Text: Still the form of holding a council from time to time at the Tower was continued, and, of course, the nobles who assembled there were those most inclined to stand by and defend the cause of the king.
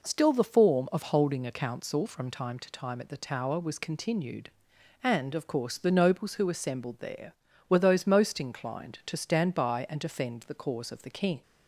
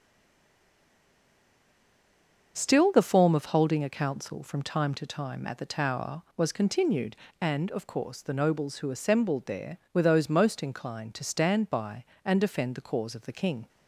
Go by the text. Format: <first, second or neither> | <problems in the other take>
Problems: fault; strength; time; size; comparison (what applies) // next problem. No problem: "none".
first | stays silent before the first word; strong; until 2.5 s; 2.5 s long // starts louder than the rest; until 3.5 s; 6.5 dB